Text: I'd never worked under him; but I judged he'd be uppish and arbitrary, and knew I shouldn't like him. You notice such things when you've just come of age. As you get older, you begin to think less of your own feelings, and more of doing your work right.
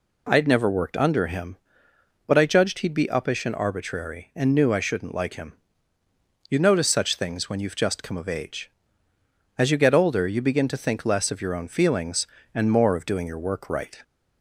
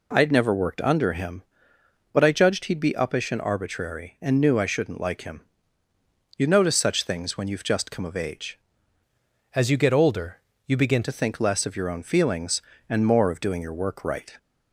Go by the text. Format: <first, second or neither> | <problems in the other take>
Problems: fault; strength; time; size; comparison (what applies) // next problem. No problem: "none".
first | changes voice from "As" to "begin"; from 9.5 to 11.0 s; 1.5 s long